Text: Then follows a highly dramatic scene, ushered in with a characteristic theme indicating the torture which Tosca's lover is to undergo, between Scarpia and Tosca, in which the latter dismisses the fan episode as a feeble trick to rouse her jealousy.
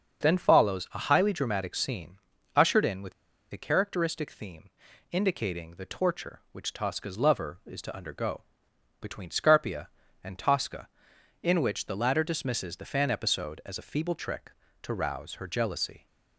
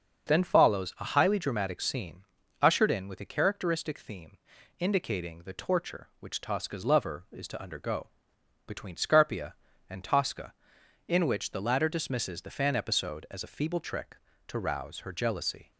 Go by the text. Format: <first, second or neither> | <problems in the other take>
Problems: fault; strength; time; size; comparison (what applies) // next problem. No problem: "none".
second | starts louder than the rest; until 1.2 s; 6.5 dB; also in the second // pauses between "with" and "a"; at 3.1 s; 0.41 s long // pauses between "theme" and "indicating"; at 4.6 s; 0.42 s long; also in the second